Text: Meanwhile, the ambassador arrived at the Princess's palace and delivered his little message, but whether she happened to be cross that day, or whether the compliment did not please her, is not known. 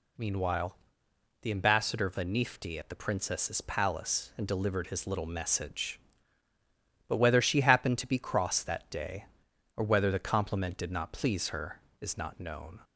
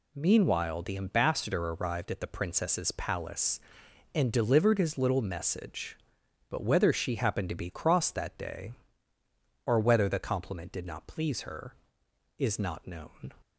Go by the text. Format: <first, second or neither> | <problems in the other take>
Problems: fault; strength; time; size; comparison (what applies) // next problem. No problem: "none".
second | says "vanifti" for "arrived"; at 2.0 s